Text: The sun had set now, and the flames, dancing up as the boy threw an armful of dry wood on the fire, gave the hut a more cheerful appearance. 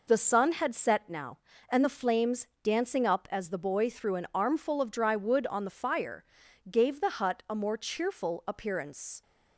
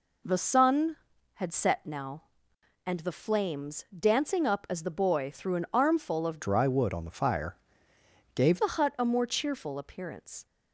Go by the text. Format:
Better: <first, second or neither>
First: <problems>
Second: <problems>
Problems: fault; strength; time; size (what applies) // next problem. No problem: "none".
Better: first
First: none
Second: changes voice from "dry" to "gave"; from 6.4 to 8.6 s; 2.2 s long